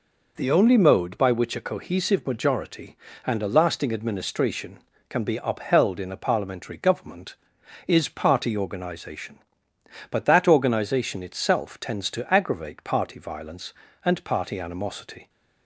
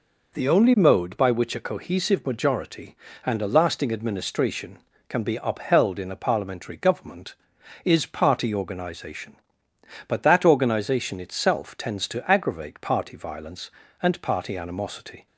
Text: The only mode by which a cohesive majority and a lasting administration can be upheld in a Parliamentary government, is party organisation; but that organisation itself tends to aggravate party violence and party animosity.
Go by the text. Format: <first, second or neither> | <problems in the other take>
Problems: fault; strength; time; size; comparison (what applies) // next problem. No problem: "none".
neither | none